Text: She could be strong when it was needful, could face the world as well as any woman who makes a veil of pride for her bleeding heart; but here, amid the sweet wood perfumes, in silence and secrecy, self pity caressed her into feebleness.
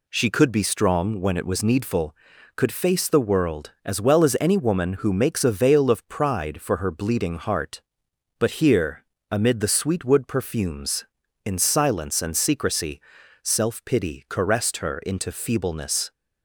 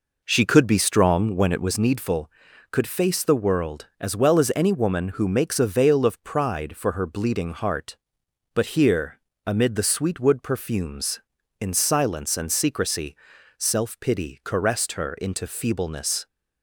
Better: first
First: none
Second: starts louder than the rest; noticeable; until 1.9 s; 4.5 dB

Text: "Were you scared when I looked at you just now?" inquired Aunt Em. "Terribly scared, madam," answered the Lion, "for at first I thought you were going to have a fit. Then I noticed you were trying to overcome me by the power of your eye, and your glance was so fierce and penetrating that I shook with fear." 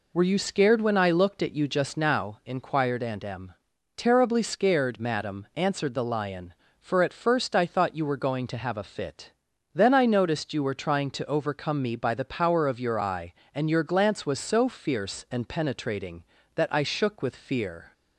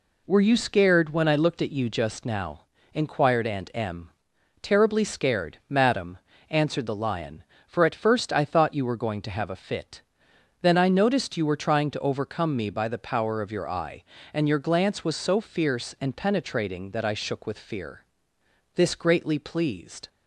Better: first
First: none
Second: goes on to say "This greatly pleased"; from 18.7 s on; 1.3 s long

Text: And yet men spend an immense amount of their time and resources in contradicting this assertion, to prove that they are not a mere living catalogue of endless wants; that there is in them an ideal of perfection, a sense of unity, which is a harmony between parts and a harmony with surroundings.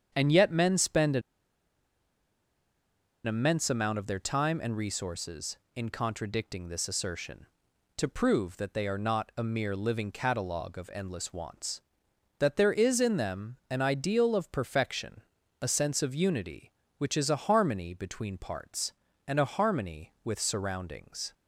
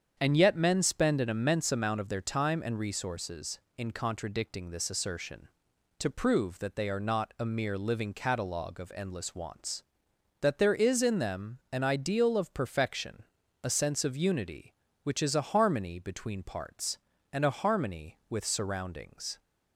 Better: second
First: starts louder than the rest; strong; until 1.1 s; 8 dB // pauses between "an" and "immense"; strong; at 1.2 s; 2.0 s long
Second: starts louder than the rest; strong; until 1.1 s; 8 dB

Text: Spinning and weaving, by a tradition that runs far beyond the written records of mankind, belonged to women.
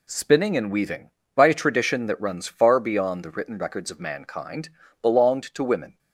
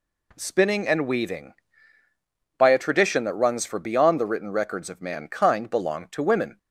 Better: first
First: none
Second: says "for" for "far"; at 3.6 s

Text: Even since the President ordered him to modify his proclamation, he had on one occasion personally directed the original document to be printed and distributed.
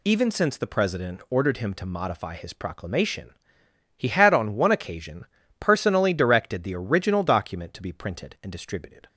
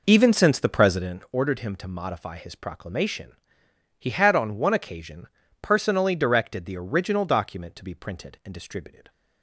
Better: first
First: pauses between "occasion" and "personally"; slight; at 5.2 s; 0.34 s long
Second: starts louder than the rest; noticeable; until 1.2 s; 5 dB // pauses between "occasion" and "personally"; slight; at 5.2 s; 0.34 s long

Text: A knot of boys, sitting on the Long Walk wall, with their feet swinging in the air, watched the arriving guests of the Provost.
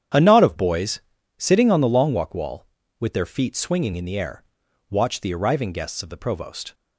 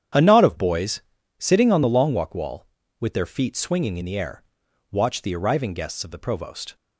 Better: neither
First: starts louder than the rest; strong; until 1.5 s; 9.5 dB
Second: starts louder than the rest; strong; until 1.5 s; 9.5 dB

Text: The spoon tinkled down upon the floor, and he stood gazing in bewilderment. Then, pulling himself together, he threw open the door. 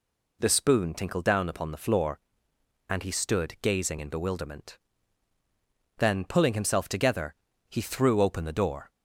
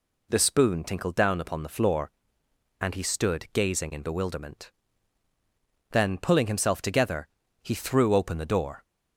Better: neither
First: none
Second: none

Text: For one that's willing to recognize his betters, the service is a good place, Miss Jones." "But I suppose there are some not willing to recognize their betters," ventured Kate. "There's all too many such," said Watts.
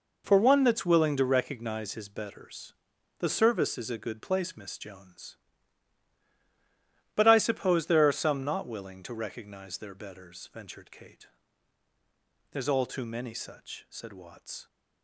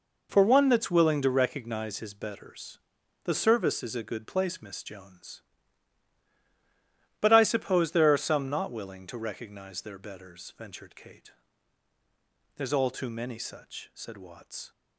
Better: neither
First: none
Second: none

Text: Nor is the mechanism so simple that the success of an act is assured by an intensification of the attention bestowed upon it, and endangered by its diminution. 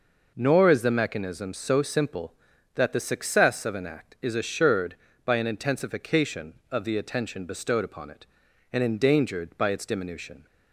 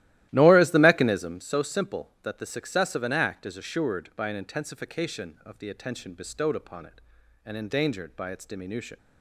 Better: first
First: none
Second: starts louder than the rest; strong; until 1.5 s; 15 dB

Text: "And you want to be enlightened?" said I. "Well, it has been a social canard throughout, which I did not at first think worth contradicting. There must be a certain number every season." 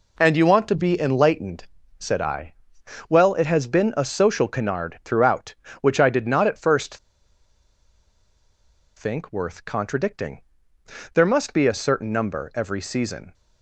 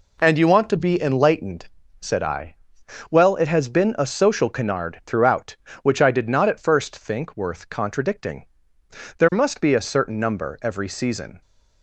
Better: second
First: pauses between "first" and "think"; strong; at 6.9 s; 2.0 s long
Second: none

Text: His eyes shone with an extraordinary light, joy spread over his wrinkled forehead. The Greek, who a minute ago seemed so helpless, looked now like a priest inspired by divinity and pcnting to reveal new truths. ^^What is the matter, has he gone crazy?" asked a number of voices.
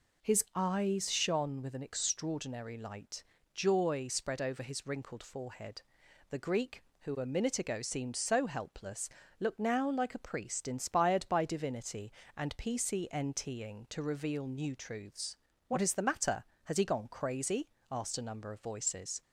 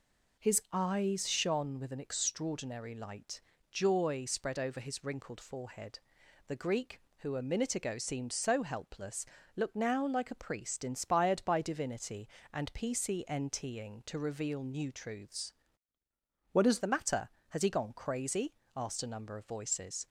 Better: first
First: none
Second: changes voice from "What" to "is"; from 16.5 to 16.7 s; 0.2 s long

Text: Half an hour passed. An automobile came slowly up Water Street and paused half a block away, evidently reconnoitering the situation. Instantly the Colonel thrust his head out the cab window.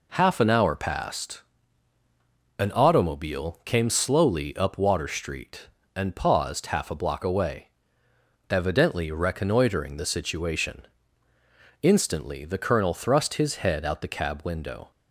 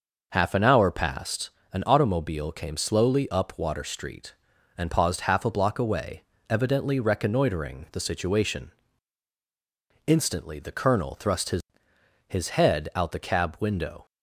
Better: first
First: none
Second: says "his" twice; at 12.2 s

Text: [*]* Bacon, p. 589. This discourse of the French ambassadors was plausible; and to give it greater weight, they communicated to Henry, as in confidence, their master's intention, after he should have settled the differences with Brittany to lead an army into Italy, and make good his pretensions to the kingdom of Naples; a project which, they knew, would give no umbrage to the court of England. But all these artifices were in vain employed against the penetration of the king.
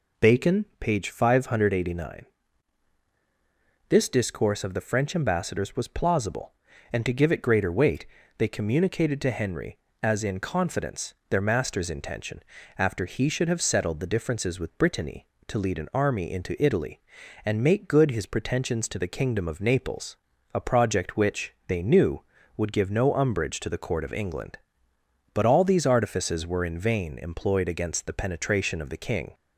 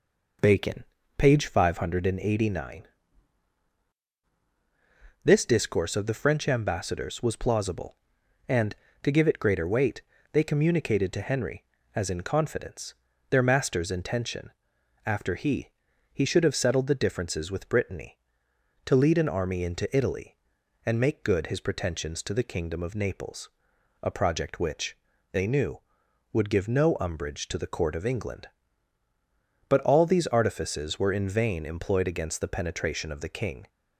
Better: first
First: none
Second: says "he" twice; at 16.0 s

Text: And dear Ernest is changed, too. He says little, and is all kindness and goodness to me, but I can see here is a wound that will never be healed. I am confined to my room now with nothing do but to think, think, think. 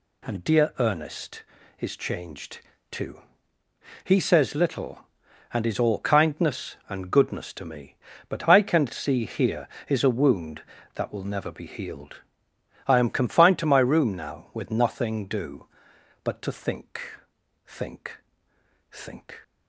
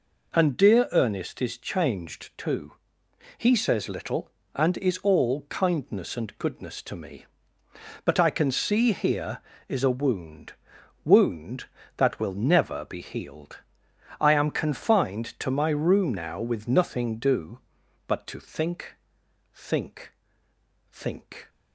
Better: first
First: none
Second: says "wound" twice; at 11.0 s

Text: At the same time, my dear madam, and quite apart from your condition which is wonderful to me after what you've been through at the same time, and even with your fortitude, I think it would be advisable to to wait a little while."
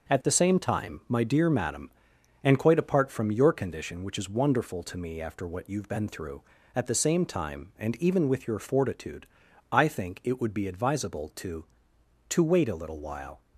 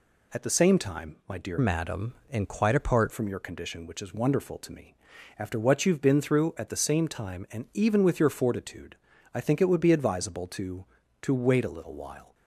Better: first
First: none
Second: changes voice from "madam" to "apart"; from 1.5 to 3.1 s; 1.6 s long // pauses between "me" and "after"; at 4.9 s; 0.42 s long

